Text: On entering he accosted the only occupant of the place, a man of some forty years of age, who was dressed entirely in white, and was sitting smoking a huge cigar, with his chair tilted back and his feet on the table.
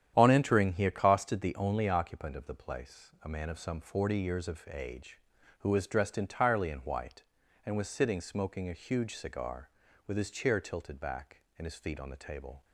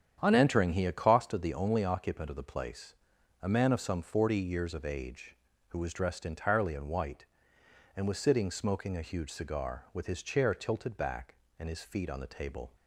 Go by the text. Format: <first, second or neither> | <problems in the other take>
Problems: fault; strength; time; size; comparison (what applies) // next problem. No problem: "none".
neither | starts louder than the rest; strong; the same in both